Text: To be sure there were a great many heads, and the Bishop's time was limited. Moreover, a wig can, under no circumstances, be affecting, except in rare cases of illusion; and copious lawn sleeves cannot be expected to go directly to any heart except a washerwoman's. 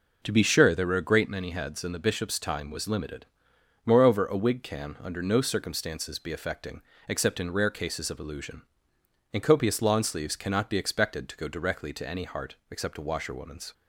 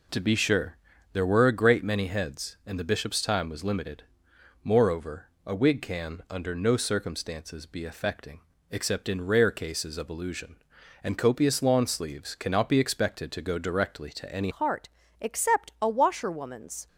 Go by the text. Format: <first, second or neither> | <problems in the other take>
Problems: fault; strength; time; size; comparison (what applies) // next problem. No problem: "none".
first | pauses between "sure" and "there"; slight; at 0.7 s; 0.36 s long // changes voice at "heart"; from 14.5 s on; 2.3 s long // pauses between "heart" and "except"; slight; at 14.8 s; 0.32 s long